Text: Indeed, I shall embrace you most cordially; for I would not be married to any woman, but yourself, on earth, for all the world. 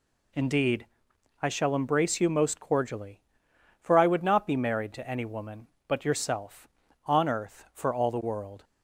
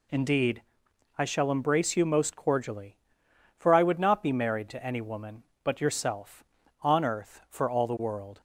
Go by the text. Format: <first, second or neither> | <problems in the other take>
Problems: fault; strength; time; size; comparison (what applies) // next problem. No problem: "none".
neither | none